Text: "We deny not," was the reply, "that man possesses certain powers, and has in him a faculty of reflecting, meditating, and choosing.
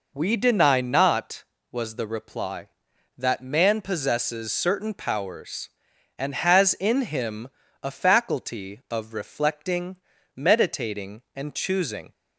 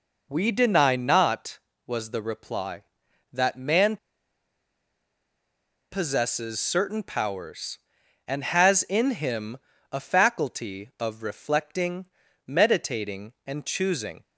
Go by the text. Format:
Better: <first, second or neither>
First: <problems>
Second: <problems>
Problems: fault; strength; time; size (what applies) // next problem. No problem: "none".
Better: first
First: pauses between "him" and "a"; slight; at 7.4 s; 0.34 s long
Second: pauses between "man" and "possesses"; strong; at 3.9 s; 1.9 s long // pauses between "him" and "a"; slight; at 9.5 s; 0.34 s long